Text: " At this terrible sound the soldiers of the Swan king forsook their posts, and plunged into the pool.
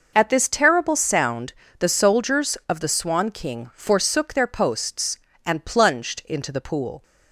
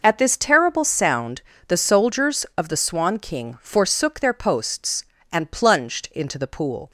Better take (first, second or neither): neither